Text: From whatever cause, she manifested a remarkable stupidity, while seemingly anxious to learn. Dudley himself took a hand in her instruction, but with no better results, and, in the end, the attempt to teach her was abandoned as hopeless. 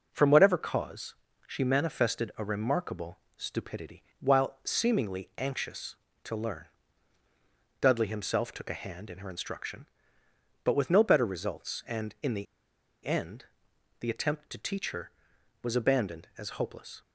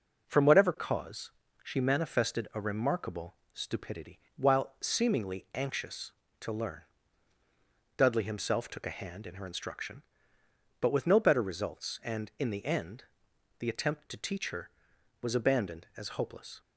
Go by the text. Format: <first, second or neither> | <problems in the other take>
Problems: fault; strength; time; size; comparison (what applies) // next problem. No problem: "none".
second | pauses between "remarkable" and "stupidity"; slight; at 3.1 s; 0.18 s long; slight in the second // pauses between "the" and "end"; noticeable; at 12.4 s; 0.61 s long